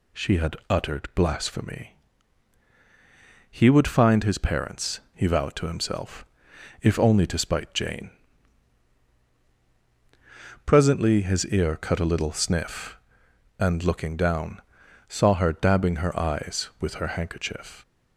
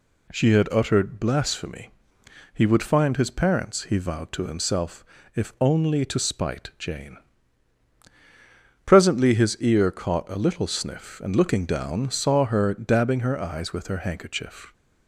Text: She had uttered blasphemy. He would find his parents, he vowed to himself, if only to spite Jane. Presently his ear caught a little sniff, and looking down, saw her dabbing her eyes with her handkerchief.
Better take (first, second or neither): second